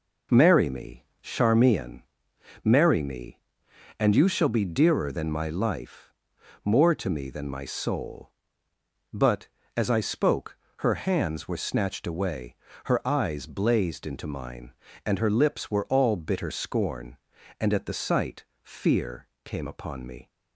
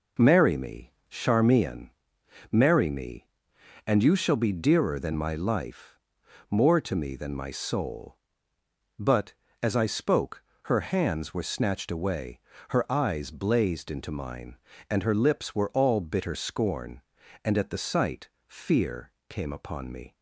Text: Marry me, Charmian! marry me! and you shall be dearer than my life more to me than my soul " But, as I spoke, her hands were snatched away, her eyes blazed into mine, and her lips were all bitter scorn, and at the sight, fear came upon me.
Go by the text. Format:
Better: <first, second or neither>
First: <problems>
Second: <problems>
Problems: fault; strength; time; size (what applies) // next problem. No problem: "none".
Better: neither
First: pauses between "life" and "more"; noticeable; at 6.1 s; 0.52 s long // pauses between "fear" and "came"; slight; at 19.2 s; 0.18 s long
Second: pauses between "life" and "more"; noticeable; at 5.9 s; 0.52 s long // pauses between "fear" and "came"; slight; at 19.1 s; 0.18 s long